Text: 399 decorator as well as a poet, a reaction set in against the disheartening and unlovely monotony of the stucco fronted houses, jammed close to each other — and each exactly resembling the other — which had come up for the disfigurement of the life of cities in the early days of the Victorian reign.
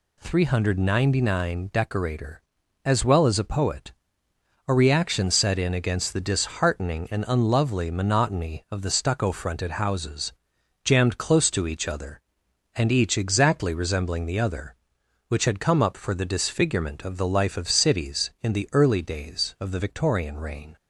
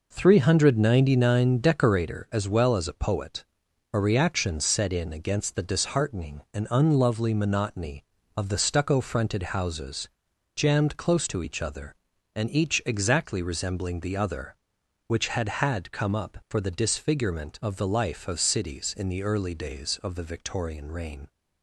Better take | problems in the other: first | says "had" twice; at 15.5 s

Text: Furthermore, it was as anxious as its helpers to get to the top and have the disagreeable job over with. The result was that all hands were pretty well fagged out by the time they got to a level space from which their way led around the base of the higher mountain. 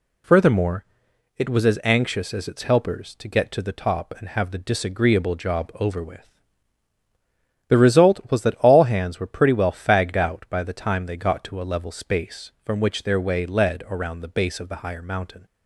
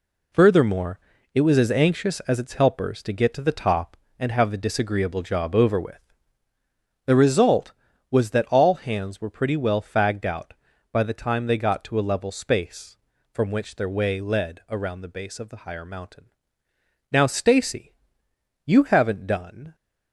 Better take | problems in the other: first | goes on to say "Now Stacy you haven't done"; strong; from 17.1 s on; 2.6 s long

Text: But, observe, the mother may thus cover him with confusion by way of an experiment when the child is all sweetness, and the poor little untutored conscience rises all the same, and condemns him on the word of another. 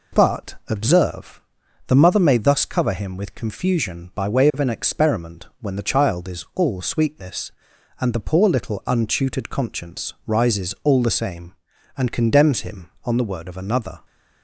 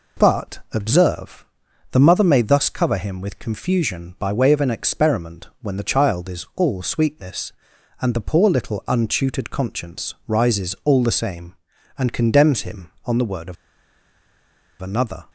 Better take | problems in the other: first | pauses between "of" and "another"; strong; at 13.5 s; 1.2 s long

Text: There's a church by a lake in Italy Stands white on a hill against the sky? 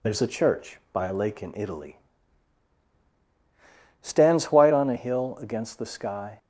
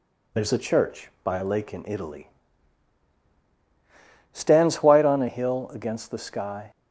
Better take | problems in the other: neither | pauses between "Italy" and "Stands"; strong; the same in both

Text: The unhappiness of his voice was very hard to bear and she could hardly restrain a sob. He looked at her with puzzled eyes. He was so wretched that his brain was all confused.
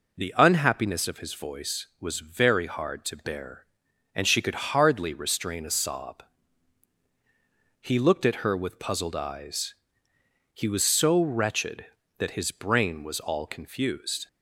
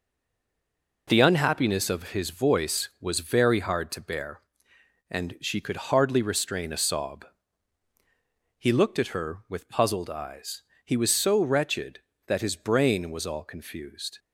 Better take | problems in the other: first | stays silent before the first word; until 1.0 s; 1.0 s long

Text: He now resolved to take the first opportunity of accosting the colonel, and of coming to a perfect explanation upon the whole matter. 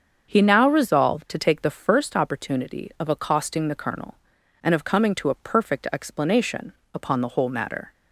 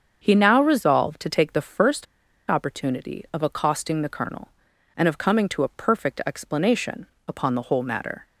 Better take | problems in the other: first | starts louder than the rest; until 1.2 s; 7 dB; also in the first // pauses between "first" and "opportunity"; at 2.0 s; 0.43 s long // pauses between "explanation" and "upon"; slight; at 7.0 s; 0.22 s long; slight in the first

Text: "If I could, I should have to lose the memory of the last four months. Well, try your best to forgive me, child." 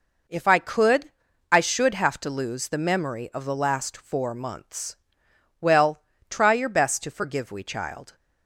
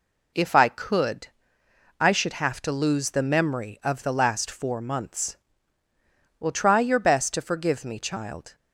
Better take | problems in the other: second | says "we" for "me"; at 7.5 s

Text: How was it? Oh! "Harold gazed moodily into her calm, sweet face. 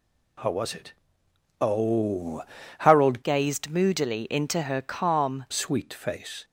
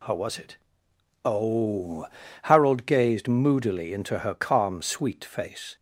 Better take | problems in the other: second | changes voice from "gazed" to "calm"; from 3.2 to 5.4 s; 2.2 s long

